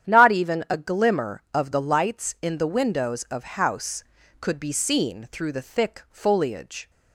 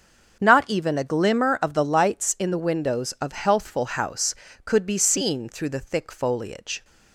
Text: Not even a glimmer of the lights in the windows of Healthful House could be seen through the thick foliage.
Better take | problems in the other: second | starts louder than the rest; strong; until 1.1 s; 9.5 dB; also in the second // skips "Healthful"; at 3.4 s

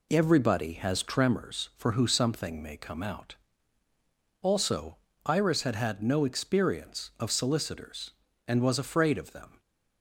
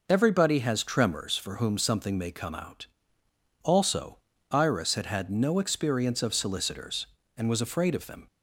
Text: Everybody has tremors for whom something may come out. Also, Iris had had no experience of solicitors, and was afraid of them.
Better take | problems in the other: second | says "who" for "whom"; at 1.9 s

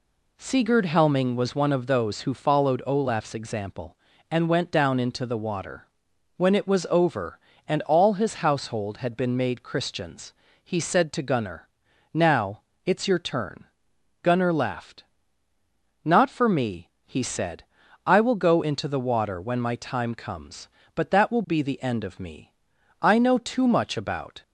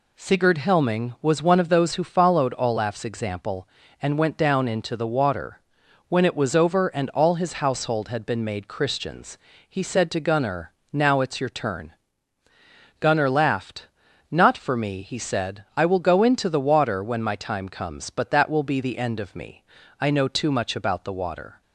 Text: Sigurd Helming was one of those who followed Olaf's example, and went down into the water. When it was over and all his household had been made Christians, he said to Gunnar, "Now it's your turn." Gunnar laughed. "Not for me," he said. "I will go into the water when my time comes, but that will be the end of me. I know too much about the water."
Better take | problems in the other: second | pauses between "Now" and "it's"; slight; at 12.5 s; 0.24 s long // stops before "the water"; at 24.4 s

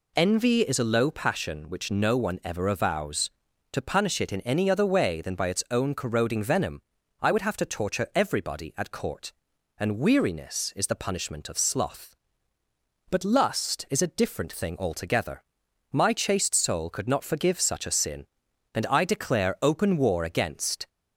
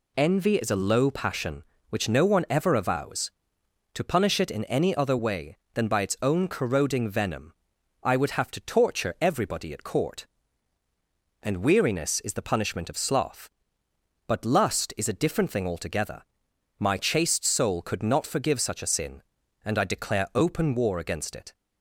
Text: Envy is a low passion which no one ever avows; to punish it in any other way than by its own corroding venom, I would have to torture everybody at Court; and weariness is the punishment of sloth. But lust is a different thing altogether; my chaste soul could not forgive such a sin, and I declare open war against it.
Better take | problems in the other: second | stops before "it"; at 20.8 s

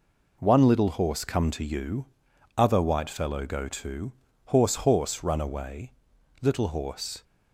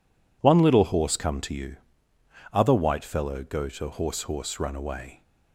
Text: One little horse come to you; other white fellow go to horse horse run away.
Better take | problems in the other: second | pauses between "to" and "horse"; slight; at 4.1 s; 0.32 s long // goes on to say "Little horse"; noticeable; from 6.4 s on; 0.82 s long

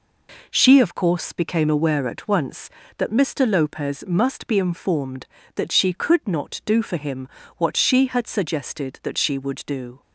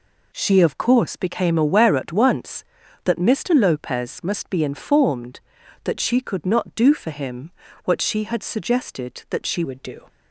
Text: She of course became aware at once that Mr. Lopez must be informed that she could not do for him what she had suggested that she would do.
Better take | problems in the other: first | pauses between "him" and "what"; slight; at 7.5 s; 0.34 s long; slight in the first // changes voice at "would"; from 9.6 s on; 0.4 s long

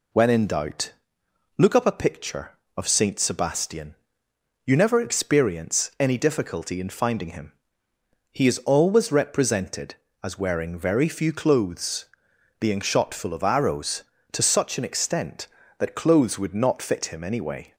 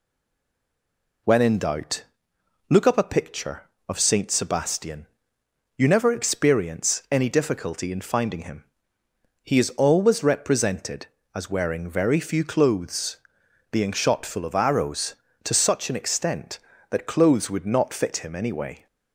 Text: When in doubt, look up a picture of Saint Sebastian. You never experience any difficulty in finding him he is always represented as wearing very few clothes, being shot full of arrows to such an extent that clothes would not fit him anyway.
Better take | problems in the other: first | stays silent before the first word; noticeable; until 1.2 s; 1.2 s long // pauses between "him" and "he"; noticeable; at 8.6 s; 0.82 s long; noticeable in the first

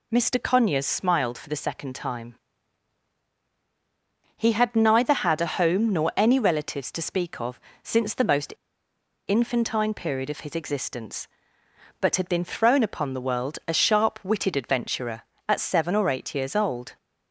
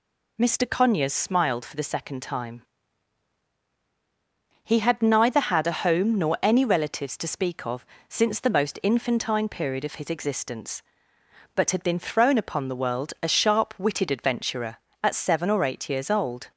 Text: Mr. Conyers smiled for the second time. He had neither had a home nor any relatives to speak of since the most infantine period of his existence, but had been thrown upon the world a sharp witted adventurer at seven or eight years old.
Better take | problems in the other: second | pauses between "of" and "since"; slight; at 7.5 s; 0.24 s long; slight in the second // pauses between "most" and "infantine"; noticeable; at 8.5 s; 0.73 s long

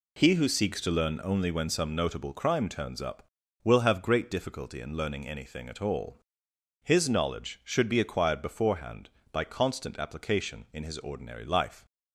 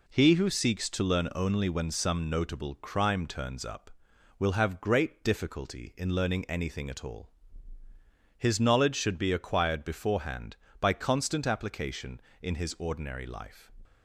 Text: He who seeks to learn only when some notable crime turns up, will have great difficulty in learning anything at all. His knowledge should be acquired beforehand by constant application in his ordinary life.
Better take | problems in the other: neither | none

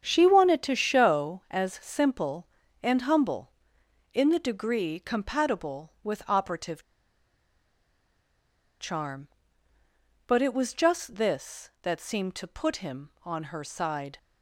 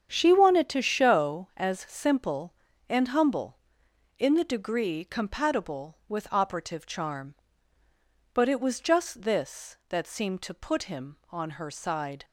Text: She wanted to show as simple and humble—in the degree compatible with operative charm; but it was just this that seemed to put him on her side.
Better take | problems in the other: second | starts louder than the rest; strong; until 1.0 s; 8 dB; strong in the second // pauses between "operative" and "charm"; strong; at 6.8 s; 1.9 s long

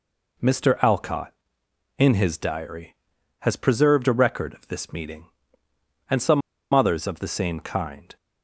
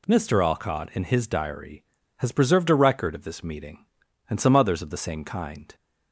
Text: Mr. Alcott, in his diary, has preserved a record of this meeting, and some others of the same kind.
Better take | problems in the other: second | pauses between "some" and "others"; slight; at 6.4 s; 0.33 s long

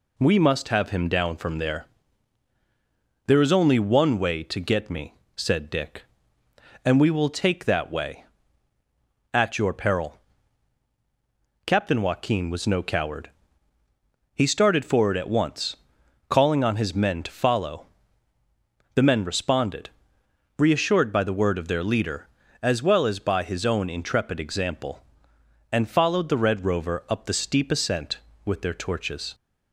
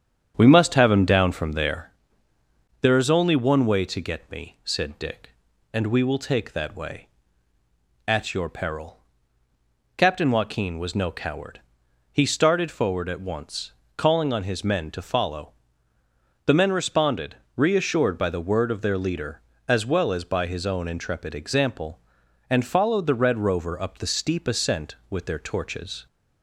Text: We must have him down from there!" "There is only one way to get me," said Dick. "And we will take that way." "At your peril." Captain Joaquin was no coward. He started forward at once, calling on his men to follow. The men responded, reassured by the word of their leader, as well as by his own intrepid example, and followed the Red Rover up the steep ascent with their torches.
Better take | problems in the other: first | starts louder than the rest; strong; until 2.0 s; 8.5 dB

